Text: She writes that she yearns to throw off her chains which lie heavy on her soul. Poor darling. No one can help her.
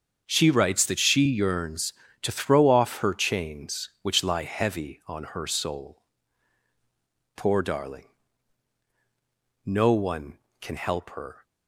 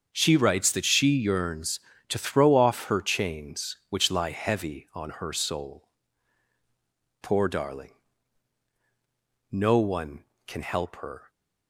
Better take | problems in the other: neither | starts louder than the rest; the same in both

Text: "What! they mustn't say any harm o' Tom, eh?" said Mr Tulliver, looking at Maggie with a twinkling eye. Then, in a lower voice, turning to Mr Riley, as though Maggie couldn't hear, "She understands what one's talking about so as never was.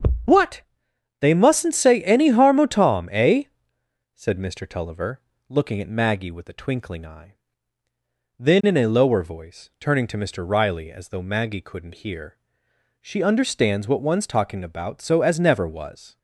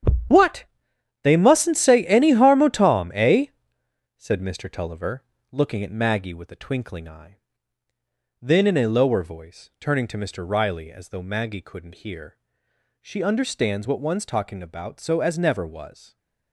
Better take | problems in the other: first | gets quieter; strong; throughout; 12.5 dB // starts louder than the rest; strong; until 1.8 s; 9 dB; also in the first

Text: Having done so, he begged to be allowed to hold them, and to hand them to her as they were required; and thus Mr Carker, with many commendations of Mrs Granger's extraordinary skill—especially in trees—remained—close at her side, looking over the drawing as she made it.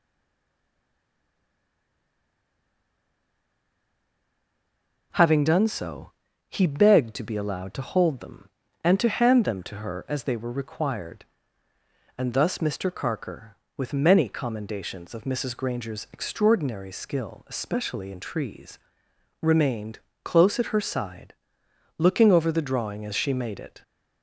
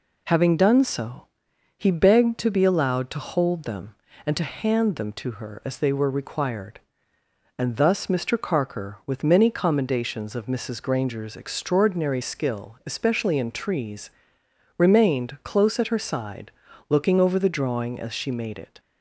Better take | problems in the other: second | stays silent before the first word; strong; until 5.1 s; 5.1 s long

